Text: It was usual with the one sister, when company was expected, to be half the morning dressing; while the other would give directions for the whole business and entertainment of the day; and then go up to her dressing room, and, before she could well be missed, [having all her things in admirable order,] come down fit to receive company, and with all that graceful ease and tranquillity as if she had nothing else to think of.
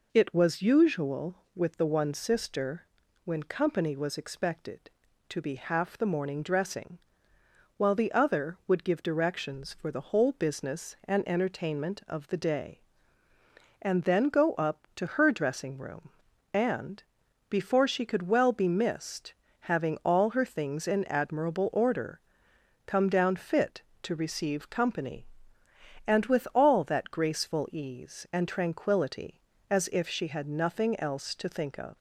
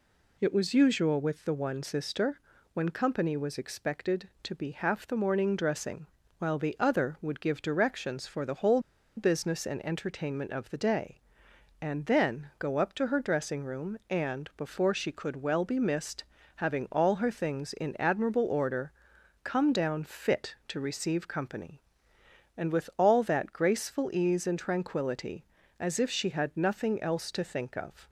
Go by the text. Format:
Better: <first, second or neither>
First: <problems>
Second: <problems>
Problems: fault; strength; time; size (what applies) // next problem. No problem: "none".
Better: first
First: none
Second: pauses between "whole" and "business"; at 8.7 s; 0.37 s long